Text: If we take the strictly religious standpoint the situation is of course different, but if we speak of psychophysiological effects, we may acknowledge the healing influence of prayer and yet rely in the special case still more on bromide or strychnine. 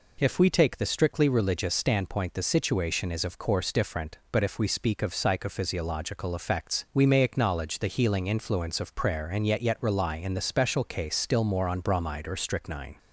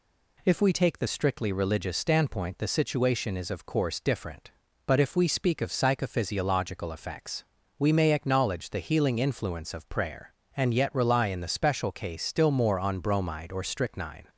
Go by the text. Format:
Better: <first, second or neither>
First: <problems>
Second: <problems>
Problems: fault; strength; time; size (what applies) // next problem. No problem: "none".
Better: second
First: says "yet" twice; at 9.6 s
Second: none